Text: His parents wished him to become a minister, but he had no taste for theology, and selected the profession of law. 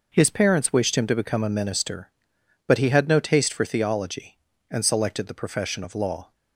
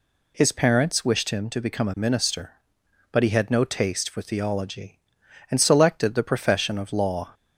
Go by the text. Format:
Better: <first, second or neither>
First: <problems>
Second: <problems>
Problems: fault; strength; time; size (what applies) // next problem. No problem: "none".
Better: neither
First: none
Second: none